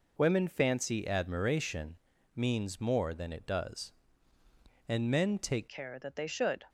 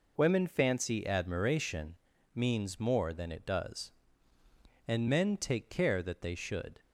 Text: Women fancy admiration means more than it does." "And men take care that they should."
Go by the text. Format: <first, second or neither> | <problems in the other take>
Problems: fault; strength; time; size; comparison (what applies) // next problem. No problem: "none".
second | pauses between "admiration" and "means"; at 1.9 s; 0.40 s long; also in the second // changes voice at "care"; from 5.6 s on; 1.0 s long